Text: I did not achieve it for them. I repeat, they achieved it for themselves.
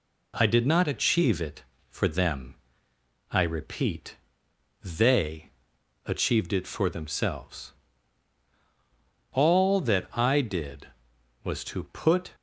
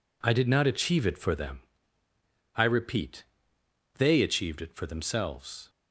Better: second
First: pauses between "they" and "achieved"; noticeable; at 5.5 s; 0.54 s long // goes on to say "All that I did was to put"; strong; from 9.3 s on; 3.0 s long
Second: none

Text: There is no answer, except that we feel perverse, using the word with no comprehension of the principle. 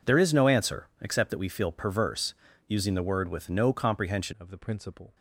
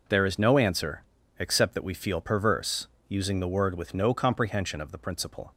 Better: second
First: changes voice at "of"; from 4.4 s on; 0.7 s long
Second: none

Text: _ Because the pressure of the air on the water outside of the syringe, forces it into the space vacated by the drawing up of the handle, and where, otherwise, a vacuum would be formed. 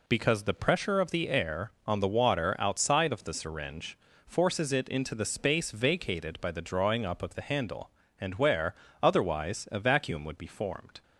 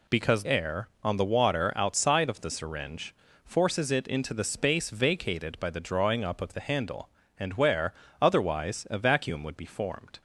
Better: first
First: none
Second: skips "the pressure of the"; at 0.4 s

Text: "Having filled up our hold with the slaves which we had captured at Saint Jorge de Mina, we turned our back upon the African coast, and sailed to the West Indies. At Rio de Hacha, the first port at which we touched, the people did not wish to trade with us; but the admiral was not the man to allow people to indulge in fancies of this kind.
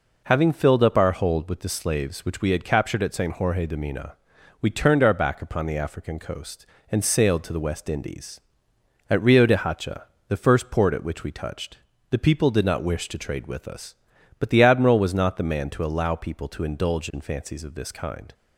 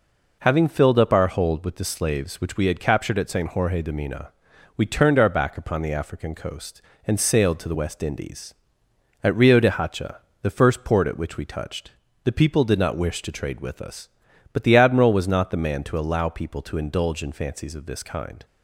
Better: neither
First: none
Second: none

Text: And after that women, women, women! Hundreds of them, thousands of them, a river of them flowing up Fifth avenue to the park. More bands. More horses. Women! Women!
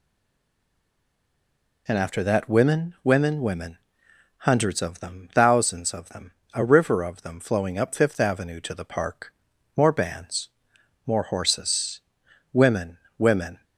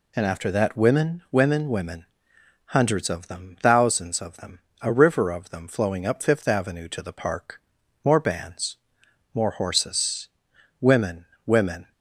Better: second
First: stays silent before the first word; noticeable; until 1.8 s; 1.8 s long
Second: none

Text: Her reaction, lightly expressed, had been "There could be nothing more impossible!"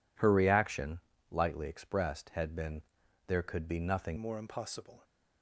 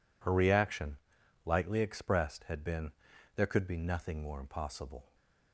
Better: second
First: pauses between "been" and "There"; noticeable; at 2.8 s; 0.46 s long // changes voice at "more"; from 4.1 s on; 0.9 s long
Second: pauses between "been" and "There"; noticeable; at 2.9 s; 0.46 s long

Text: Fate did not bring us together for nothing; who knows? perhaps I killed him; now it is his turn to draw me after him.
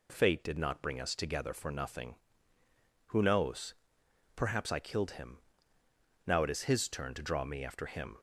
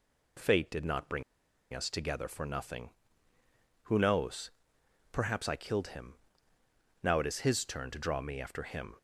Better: first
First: none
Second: pauses between "bring" and "us"; noticeable; at 1.2 s; 0.52 s long

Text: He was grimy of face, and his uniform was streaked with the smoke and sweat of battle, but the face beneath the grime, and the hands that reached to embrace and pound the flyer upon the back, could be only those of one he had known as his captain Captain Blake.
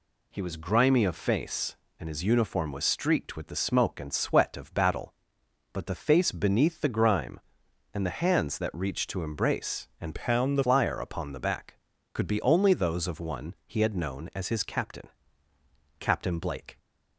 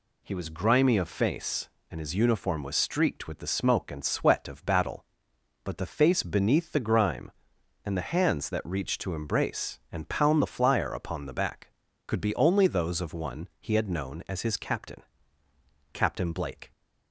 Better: second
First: changes voice from "pound" to "the"; from 10.1 to 10.6 s; 0.5 s long // pauses between "captain" and "Captain"; noticeable; at 15.0 s; 0.92 s long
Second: pauses between "captain" and "Captain"; noticeable; at 15.0 s; 0.92 s long

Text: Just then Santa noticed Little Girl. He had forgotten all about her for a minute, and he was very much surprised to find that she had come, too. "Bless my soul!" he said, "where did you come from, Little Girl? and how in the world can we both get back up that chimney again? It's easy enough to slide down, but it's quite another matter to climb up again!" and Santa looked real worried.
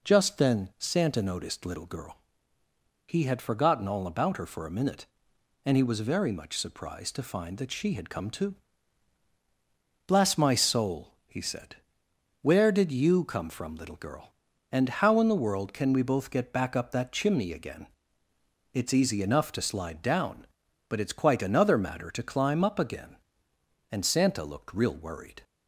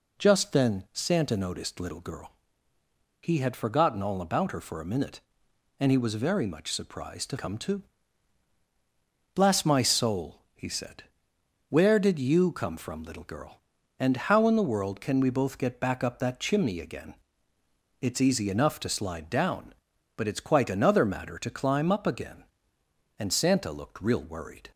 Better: first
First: none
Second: skips "find that she had"; at 7.3 s

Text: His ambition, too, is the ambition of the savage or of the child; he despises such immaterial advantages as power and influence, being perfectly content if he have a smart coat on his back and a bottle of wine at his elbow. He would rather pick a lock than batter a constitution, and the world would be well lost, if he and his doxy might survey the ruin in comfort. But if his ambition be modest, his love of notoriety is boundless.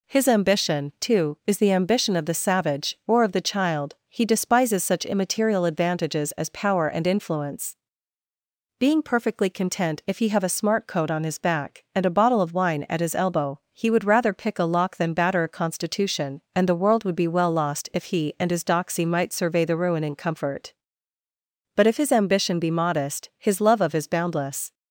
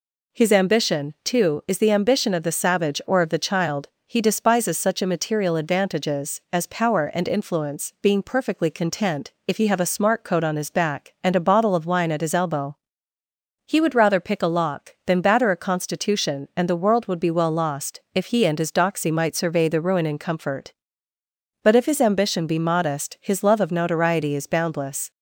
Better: second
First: skips "notoriety"; at 23.9 s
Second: none

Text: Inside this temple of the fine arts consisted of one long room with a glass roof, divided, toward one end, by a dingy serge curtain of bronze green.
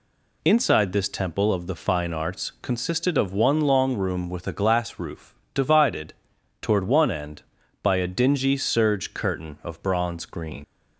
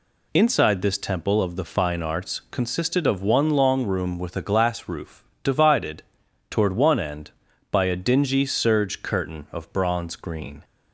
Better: second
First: leaves "green" unfinished; at 10.6 s; 90 ms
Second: none

